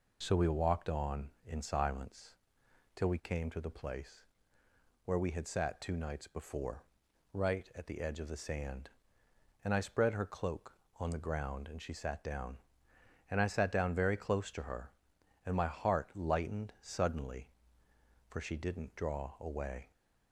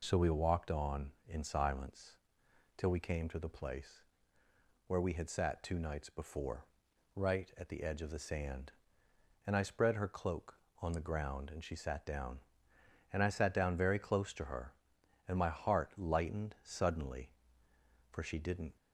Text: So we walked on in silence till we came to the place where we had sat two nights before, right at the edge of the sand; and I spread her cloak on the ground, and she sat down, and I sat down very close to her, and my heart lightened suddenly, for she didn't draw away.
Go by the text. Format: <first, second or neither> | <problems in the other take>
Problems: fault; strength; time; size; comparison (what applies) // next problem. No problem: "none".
first | pauses between "silence" and "till"; noticeable; at 2.1 s; 0.60 s long; noticeable in the first // pauses between "place" and "where"; noticeable; at 4.0 s; 0.83 s long; noticeable in the first // stops before "draw away"; at 18.7 s